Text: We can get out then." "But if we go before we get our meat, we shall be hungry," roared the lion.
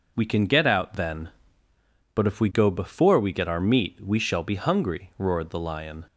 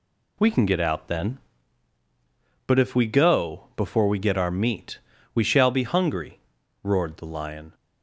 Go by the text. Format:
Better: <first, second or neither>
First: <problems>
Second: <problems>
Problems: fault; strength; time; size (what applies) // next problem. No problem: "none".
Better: neither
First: none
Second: none